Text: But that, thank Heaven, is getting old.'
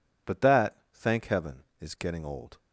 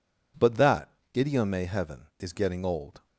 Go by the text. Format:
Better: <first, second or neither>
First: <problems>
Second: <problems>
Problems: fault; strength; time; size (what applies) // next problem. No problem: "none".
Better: first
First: none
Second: says "idiome" for "thank"; at 1.1 s